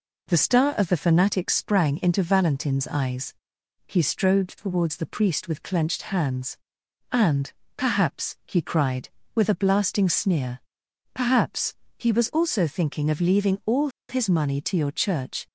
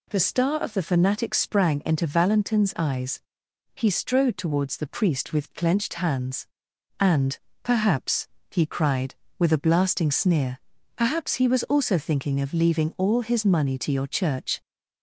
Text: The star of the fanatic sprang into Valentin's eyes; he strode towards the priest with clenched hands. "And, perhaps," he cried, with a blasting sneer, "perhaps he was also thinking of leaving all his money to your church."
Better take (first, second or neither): second